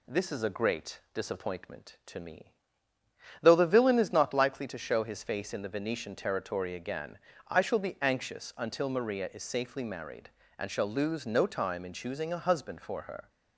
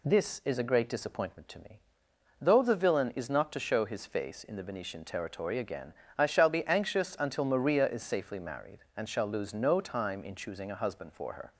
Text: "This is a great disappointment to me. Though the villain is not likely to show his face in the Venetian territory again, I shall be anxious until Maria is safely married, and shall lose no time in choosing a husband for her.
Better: first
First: none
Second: skips "likely"; at 3.5 s

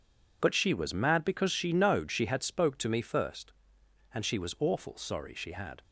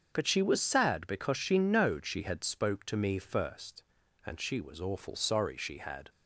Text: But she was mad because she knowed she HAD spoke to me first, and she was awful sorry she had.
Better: first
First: none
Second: starts louder than the rest; until 1.1 s; 7 dB // says "sad" for "mad"; at 0.5 s

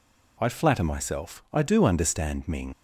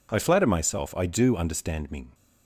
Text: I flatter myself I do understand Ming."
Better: second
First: leaves "Ming" unfinished; at 2.7 s; 75 ms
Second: none

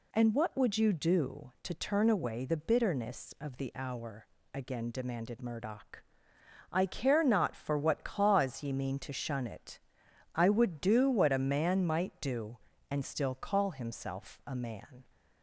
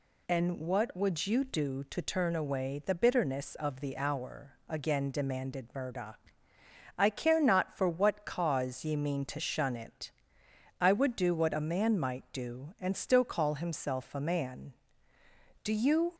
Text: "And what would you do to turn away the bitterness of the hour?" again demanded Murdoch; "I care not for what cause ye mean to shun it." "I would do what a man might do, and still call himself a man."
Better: first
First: none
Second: goes on to say "Do you"; from 15.6 s on; 0.50 s long

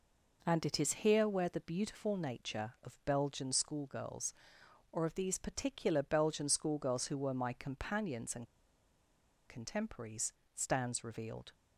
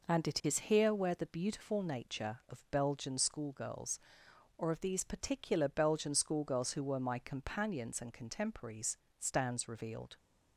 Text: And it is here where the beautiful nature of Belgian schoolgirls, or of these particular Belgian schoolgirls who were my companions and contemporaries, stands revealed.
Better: second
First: pauses between "and" and "contemporaries"; at 8.4 s; 1.0 s long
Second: none

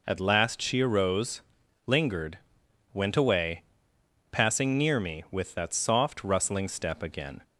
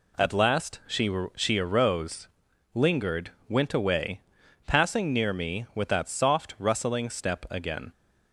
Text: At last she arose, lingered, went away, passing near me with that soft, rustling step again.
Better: first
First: none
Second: says "she" twice; at 1.3 s

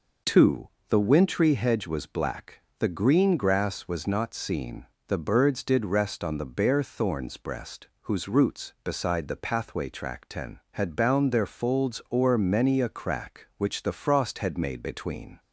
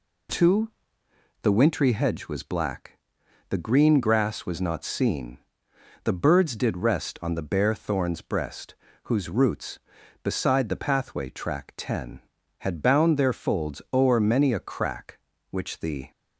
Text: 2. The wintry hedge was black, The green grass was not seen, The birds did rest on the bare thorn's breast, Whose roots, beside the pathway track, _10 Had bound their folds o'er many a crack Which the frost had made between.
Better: first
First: none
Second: stops before "frost had made between"; at 16.1 s

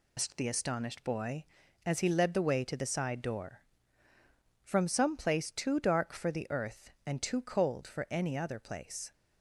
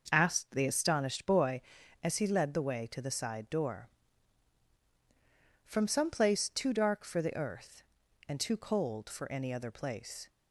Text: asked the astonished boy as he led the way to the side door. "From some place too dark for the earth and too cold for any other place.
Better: second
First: loses the start of "asked"; at 0.1 s; 130 ms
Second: none

